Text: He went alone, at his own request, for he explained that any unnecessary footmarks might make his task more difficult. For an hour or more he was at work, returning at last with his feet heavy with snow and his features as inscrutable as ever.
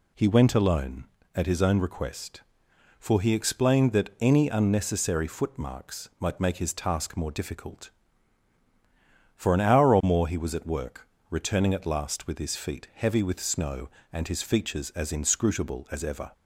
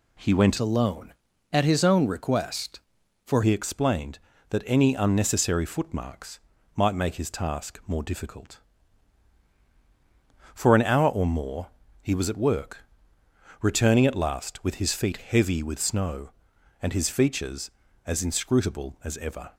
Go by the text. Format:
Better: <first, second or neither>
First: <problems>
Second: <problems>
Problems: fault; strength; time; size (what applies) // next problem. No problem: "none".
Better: first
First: none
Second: changes voice from "alone" to "for"; from 0.5 to 3.4 s; 2.9 s long // pauses between "footmarks" and "might"; slight; at 6.4 s; 0.36 s long // pauses between "more" and "he"; slight; at 11.6 s; 0.34 s long